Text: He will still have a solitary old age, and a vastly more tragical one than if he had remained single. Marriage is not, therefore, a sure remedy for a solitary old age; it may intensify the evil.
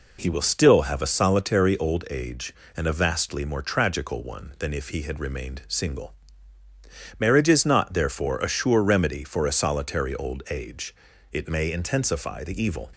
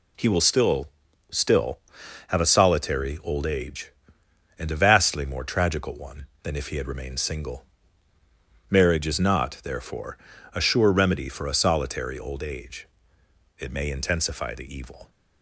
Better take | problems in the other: first | says "still" twice; at 1.2 s

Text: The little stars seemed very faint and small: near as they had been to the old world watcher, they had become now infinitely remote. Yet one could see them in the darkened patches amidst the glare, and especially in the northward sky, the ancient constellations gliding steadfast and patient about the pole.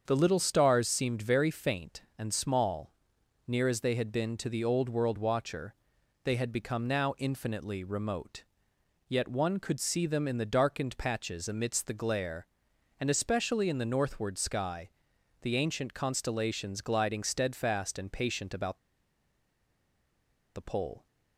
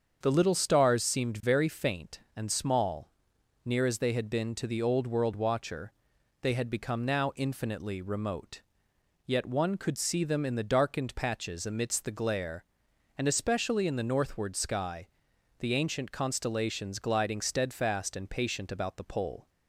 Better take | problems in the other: second | starts louder than the rest; until 1.0 s; 7 dB; also in the second // pauses between "about" and "the"; strong; at 18.7 s; 1.7 s long

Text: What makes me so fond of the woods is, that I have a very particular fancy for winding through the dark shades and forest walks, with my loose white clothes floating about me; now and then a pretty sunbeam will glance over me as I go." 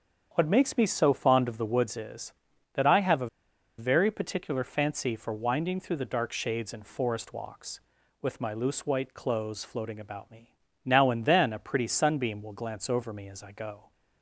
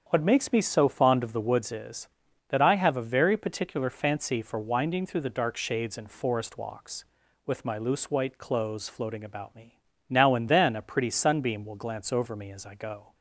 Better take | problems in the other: second | starts louder than the rest; strong; until 1.3 s; 7.5 dB; strong in the second // pauses between "a" and "very"; noticeable; at 3.2 s; 0.52 s long

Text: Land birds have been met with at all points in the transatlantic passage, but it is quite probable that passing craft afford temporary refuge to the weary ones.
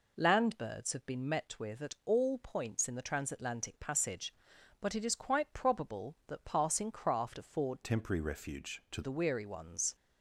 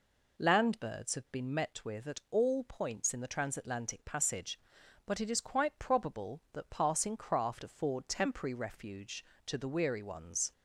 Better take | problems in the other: second | changes voice from "temporary" to "to"; from 7.8 to 9.0 s; 1.2 s long

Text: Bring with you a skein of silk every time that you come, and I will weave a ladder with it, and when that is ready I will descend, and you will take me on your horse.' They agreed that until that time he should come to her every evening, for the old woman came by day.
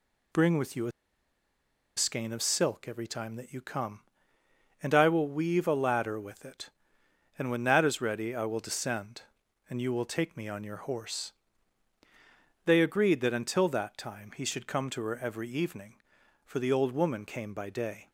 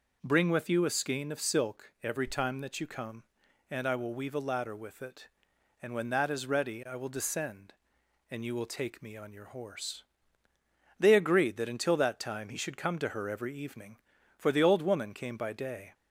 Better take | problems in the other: second | pauses between "a" and "skein"; at 0.9 s; 1.0 s long

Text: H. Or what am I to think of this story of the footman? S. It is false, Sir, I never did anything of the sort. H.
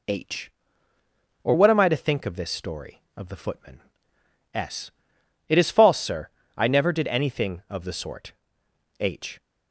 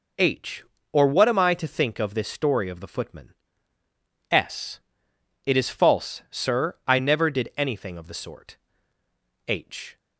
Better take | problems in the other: neither | none

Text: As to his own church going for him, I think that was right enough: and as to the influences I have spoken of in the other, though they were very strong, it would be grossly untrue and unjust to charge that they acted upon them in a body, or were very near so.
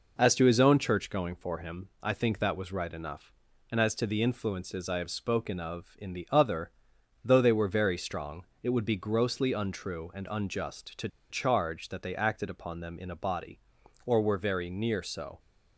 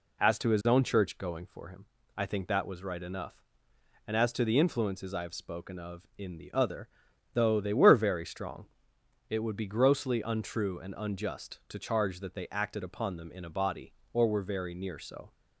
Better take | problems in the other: second | pauses between "to" and "charge"; slight; at 11.0 s; 0.22 s long

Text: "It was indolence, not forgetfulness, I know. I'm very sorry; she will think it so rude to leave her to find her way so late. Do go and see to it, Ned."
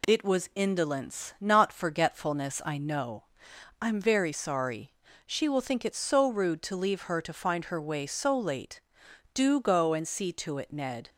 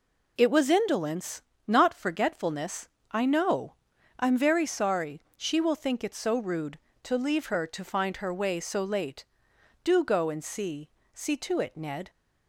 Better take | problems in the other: first | says "see" twice; at 11.1 s

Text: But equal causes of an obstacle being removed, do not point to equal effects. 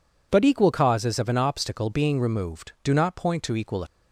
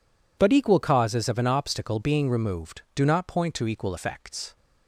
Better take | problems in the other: second | stops before "effects"; at 3.8 s

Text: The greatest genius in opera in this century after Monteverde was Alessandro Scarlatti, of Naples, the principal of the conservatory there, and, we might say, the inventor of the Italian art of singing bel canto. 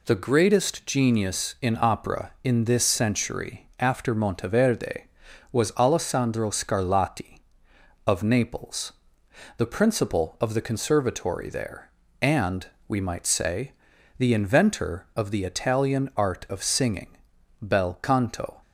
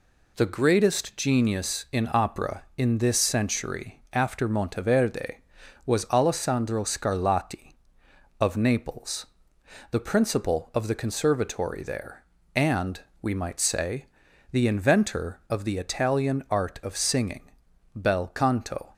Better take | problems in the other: neither | pauses between "singing" and "bel"; the same in both

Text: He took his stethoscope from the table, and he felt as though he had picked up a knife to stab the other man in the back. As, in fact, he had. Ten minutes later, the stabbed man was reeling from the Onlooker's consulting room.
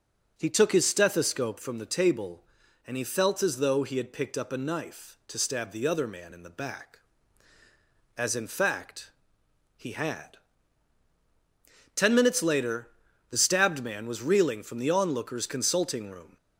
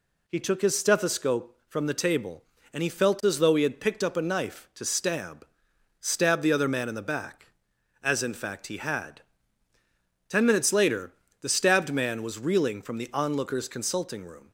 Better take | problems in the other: first | says "stab" twice; at 6.0 s

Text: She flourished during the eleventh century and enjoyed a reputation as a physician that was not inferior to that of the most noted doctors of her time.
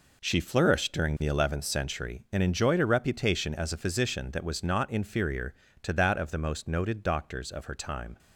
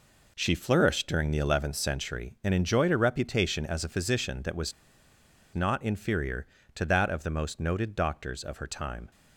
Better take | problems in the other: first | pauses between "was" and "not"; noticeable; at 4.7 s; 0.82 s long

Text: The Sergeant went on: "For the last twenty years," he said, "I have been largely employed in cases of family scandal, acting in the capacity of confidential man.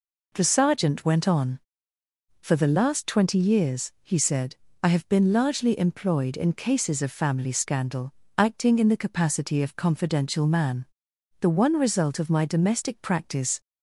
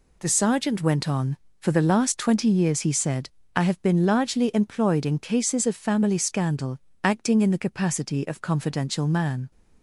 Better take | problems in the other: second | goes on to say "The one result of my domestic practice"; strong; from 11.4 s on; 2.2 s long

